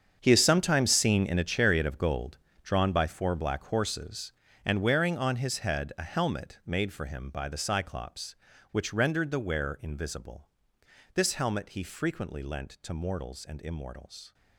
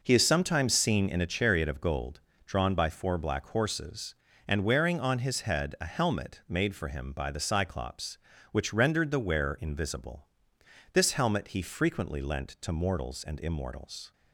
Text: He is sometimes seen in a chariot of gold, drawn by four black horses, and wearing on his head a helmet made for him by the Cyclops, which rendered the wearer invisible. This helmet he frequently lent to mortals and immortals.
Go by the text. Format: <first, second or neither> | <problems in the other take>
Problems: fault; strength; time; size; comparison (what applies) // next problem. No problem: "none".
second | gets quieter; strong; throughout; 14 dB